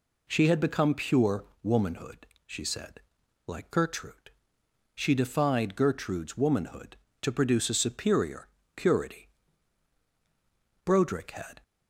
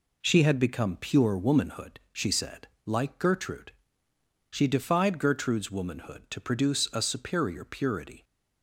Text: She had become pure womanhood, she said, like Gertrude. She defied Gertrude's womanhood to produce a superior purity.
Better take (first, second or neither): second